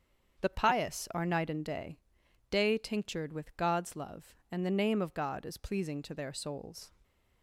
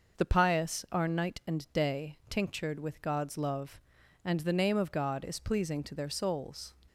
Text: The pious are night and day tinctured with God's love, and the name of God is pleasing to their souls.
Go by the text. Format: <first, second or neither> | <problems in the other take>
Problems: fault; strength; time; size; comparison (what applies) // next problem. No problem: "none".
second | starts louder than the rest; strong; until 1.4 s; 8 dB; noticeable in the second // says "day" twice; at 2.5 s